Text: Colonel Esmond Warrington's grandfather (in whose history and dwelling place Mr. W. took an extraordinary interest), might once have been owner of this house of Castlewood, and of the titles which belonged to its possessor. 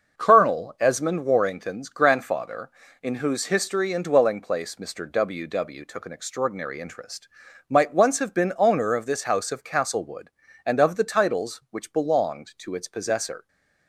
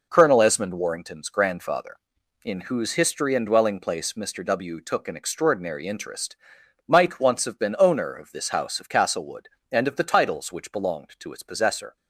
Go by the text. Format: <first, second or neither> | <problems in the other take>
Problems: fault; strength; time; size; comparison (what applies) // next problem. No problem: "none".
second | starts louder than the rest; noticeable; until 1.2 s; 6 dB // says "W" twice; at 5.4 s